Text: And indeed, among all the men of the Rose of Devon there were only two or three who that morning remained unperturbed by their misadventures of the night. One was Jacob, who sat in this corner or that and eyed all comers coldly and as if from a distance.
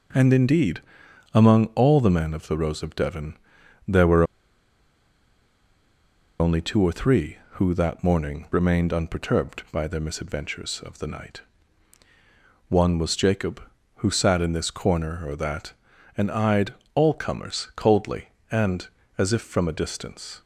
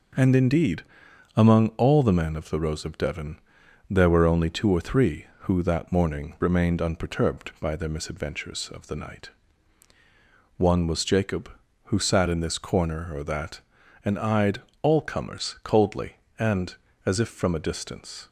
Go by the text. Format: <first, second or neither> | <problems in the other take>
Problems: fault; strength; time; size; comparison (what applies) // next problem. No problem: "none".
second | pauses between "Devon" and "there"; noticeable; at 3.3 s; 0.50 s long; noticeable in the second // pauses between "were" and "only"; strong; at 4.2 s; 2.1 s long // pauses between "eyed" and "all"; slight; at 16.7 s; 0.22 s long; slight in the second